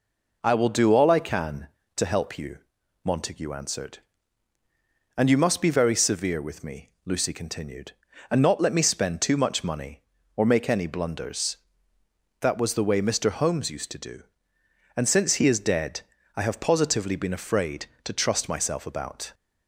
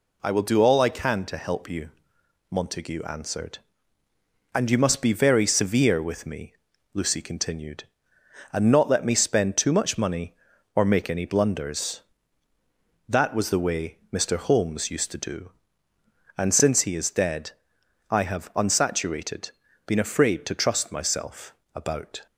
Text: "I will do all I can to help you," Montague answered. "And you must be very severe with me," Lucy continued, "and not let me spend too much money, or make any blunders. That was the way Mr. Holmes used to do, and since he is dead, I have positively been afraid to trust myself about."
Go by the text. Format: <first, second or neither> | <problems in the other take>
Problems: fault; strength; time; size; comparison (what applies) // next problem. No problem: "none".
first | says "unsaturated" for "positively"; at 18.5 s // pauses between "myself" and "about"; slight; at 21.5 s; 0.20 s long